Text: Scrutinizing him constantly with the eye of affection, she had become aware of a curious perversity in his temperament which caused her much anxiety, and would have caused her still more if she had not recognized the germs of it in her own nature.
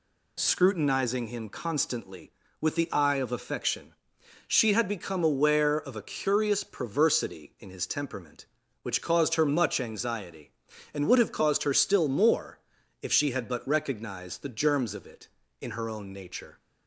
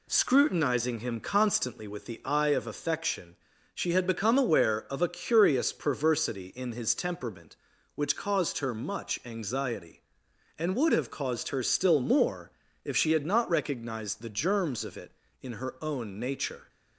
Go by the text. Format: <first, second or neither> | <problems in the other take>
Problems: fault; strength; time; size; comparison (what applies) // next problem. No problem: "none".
second | pauses between "more" and "if"; at 12.6 s; 0.42 s long; slight in the second // says "but" for "not"; at 13.4 s